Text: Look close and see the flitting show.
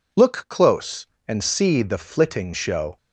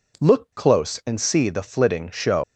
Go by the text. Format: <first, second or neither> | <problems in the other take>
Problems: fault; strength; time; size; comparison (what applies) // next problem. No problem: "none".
first | leaves "show" unfinished; at 2.4 s; 125 ms